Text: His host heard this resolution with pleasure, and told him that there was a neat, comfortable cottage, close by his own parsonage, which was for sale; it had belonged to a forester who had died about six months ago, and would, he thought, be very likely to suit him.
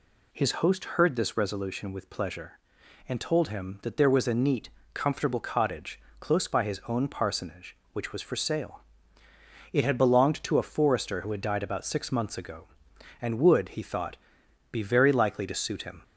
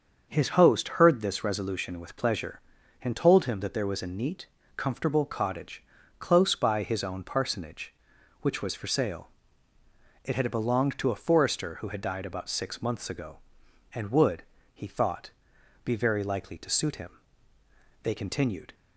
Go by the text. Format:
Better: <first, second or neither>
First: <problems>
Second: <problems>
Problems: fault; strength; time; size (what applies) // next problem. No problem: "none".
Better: first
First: none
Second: starts louder than the rest; until 1.3 s; 6.5 dB // goes on to say "They continued"; noticeable; from 18.0 s on; 0.70 s long